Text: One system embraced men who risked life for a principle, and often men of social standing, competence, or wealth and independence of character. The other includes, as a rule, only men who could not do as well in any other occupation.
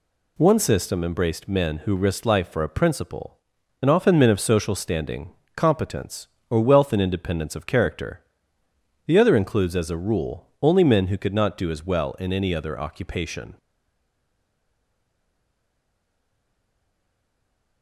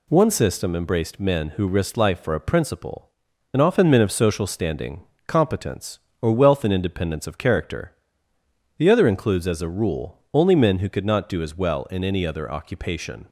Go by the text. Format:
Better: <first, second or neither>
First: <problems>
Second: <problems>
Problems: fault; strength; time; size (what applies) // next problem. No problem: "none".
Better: second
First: stays silent after the last word; strong; from 13.5 s on; 4.3 s long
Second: none